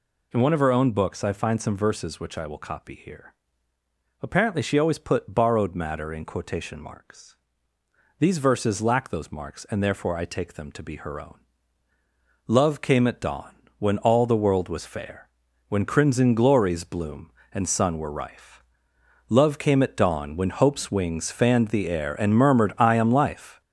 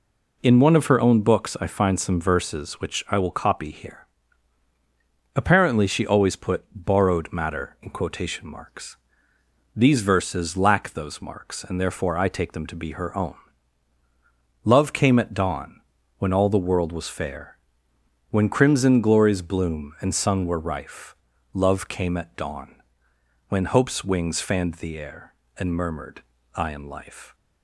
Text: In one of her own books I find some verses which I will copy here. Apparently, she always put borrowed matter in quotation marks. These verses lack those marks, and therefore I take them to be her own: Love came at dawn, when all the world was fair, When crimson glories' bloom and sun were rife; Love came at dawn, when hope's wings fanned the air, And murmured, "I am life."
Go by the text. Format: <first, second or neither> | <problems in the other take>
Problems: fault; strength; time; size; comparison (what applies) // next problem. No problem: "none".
second | gets louder; noticeable; throughout; 5.5 dB